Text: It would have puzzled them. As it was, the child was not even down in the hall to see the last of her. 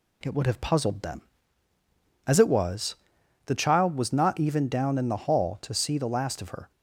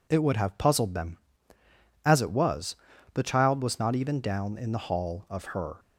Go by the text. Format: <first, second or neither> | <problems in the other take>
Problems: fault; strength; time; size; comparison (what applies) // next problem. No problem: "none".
first | skips "to see the last"; at 5.2 s